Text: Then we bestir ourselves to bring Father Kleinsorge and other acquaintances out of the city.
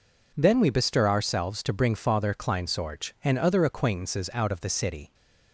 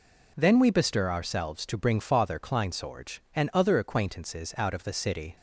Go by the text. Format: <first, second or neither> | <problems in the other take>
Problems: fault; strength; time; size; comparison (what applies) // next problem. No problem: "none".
neither | none